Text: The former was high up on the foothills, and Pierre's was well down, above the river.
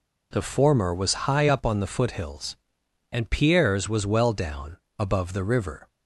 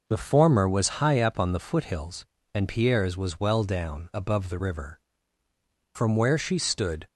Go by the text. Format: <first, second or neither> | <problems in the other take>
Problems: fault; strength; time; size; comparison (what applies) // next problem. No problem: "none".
first | goes on to say "From where she stood"; noticeable; from 5.9 s on; 1.1 s long